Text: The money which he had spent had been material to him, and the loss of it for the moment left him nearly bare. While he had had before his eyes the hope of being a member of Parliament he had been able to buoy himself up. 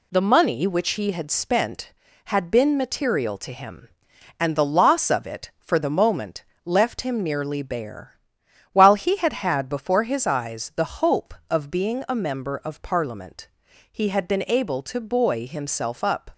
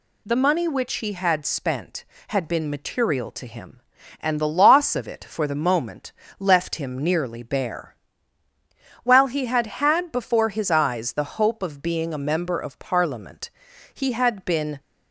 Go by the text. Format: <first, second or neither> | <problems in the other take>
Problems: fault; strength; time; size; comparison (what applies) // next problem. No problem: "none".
first | pauses between "moment" and "left"; slight; at 6.1 s; 0.26 s long; slight in the first // pauses between "Parliament" and "he"; at 13.4 s; 0.44 s long; also in the first // stops before "able to buoy himself up"; at 14.7 s